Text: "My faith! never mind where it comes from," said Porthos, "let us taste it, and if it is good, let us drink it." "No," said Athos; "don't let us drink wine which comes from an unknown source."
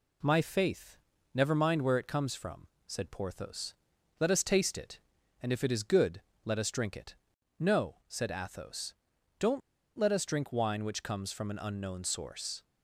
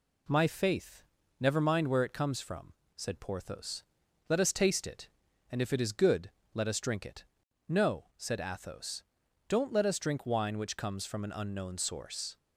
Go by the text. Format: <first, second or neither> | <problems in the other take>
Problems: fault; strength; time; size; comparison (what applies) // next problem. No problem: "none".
second | pauses between "don't" and "let"; at 9.6 s; 0.38 s long